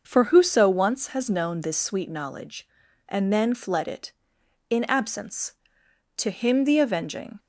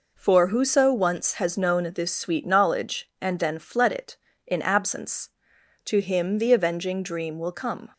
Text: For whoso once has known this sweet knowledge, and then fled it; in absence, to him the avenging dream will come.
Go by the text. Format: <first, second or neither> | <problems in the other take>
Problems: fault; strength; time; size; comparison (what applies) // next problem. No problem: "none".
second | starts louder than the rest; until 1.0 s; 6 dB // stops before "dream will come"; at 7.3 s